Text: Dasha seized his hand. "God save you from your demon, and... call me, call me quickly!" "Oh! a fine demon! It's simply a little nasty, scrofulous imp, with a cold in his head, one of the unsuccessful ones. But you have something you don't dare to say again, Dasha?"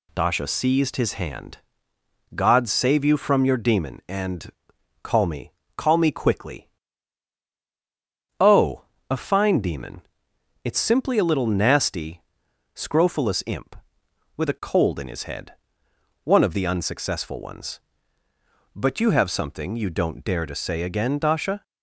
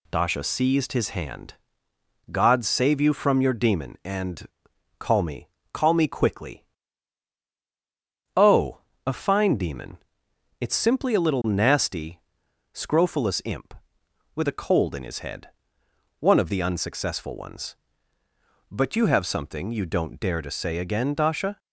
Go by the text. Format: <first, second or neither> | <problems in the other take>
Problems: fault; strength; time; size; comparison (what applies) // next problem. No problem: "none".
neither | none